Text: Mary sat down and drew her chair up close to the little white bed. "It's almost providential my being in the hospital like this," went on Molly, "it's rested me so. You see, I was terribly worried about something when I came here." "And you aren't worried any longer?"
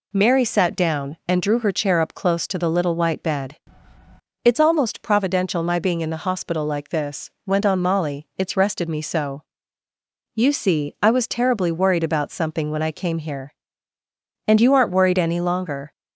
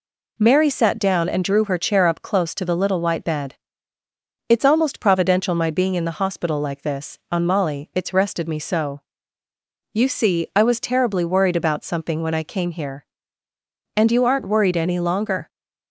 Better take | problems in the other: first | skips "went"; at 7.2 s

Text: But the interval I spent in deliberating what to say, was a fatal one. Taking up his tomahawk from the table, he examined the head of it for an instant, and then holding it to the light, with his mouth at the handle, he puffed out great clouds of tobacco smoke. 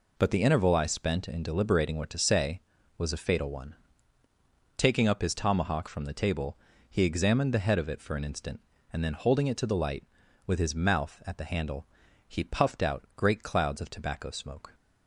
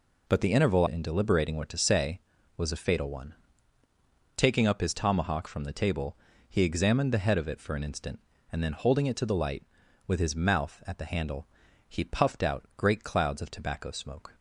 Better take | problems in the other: first | skips "I spent"; at 0.8 s

